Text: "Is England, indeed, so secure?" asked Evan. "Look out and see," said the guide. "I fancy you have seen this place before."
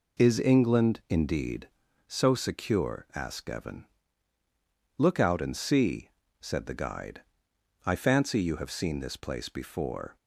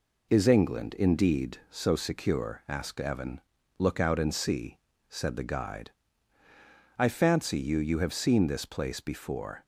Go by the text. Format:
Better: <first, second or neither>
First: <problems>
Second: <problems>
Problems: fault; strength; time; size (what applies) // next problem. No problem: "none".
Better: first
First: none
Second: says "you" twice; at 7.7 s